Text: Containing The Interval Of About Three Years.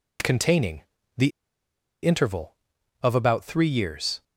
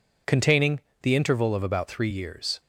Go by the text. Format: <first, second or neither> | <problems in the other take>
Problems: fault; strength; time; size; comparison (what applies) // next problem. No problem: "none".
second | pauses between "Containing" and "The"; slight; at 0.8 s; 0.34 s long; slight in the second // pauses between "The" and "Interval"; noticeable; at 1.3 s; 0.74 s long